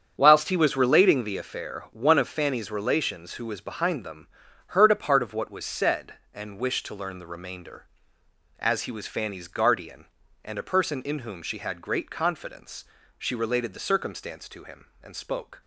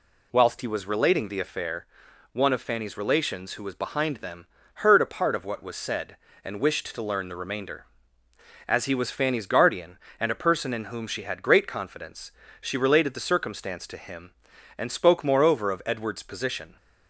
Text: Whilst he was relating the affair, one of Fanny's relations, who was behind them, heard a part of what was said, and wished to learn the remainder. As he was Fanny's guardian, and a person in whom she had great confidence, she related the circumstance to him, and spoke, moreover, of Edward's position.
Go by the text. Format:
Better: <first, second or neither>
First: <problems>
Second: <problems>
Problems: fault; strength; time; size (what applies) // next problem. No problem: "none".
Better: second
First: starts louder than the rest; strong; until 1.1 s; 8 dB // stops before "moreover of Edward's position"; at 15.6 s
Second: none